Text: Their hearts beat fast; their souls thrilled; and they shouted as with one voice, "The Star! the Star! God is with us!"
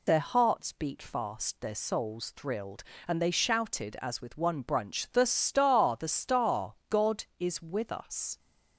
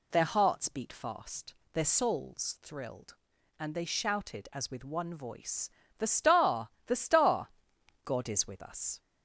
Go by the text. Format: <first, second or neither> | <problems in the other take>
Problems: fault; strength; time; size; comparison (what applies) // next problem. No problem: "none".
second | says "brunch" for "voice"; at 4.6 s